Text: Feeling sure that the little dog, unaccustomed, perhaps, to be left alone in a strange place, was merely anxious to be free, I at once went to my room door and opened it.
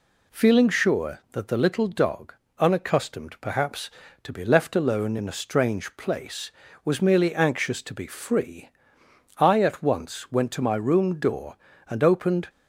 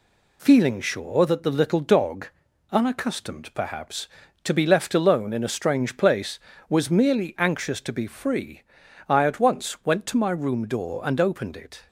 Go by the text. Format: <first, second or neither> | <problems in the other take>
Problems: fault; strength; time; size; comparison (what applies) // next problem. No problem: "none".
second | stops before "it"; at 12.4 s